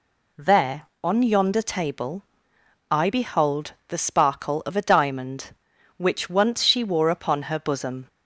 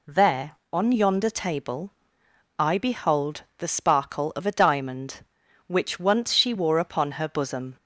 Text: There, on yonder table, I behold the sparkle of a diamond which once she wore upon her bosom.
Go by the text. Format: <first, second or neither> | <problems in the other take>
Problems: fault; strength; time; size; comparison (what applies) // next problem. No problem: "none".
neither | pauses between "behold" and "the"; slight; the same in both